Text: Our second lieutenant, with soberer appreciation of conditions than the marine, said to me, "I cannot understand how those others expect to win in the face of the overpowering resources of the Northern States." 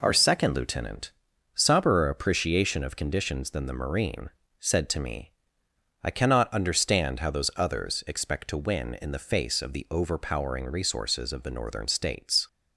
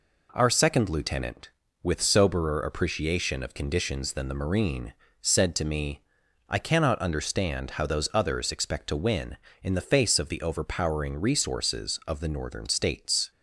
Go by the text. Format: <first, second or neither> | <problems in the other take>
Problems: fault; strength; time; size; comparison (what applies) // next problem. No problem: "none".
second | skips "with"; at 1.3 s